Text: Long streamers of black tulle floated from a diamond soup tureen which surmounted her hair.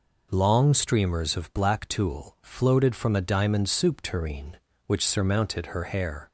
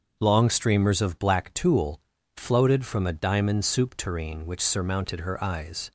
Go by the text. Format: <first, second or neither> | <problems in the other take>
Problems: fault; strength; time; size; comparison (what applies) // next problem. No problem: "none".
first | starts louder than the rest; until 1.2 s; 6.5 dB // pauses between "tulle" and "floated"; at 1.9 s; 0.38 s long // says "eyes" for "hair"; at 5.4 s